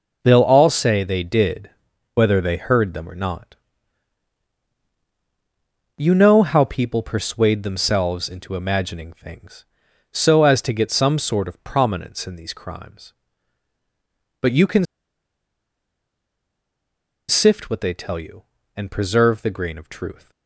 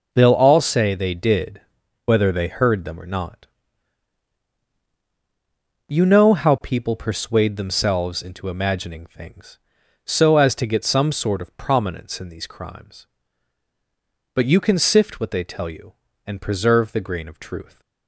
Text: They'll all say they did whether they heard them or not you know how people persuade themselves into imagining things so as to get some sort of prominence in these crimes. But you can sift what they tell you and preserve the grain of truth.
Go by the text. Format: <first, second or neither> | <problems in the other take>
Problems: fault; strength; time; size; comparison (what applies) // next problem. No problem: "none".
second | pauses between "did" and "whether"; at 1.7 s; 0.42 s long; also in the second // pauses between "not" and "you"; strong; at 3.5 s; 2.4 s long; strong in the second // pauses between "can" and "sift"; strong; at 14.8 s; 2.4 s long